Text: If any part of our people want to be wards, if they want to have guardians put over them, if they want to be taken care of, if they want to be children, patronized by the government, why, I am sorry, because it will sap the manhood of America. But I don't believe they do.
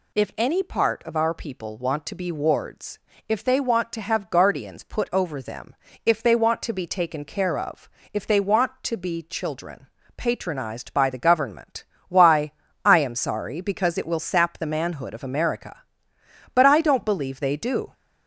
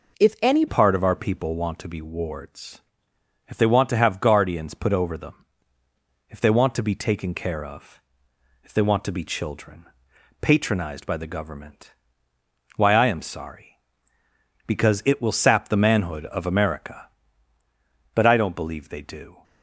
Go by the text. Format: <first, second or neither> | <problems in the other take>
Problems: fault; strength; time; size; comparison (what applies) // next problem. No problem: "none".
first | changes voice at "part"; from 0.6 s on; 18.8 s long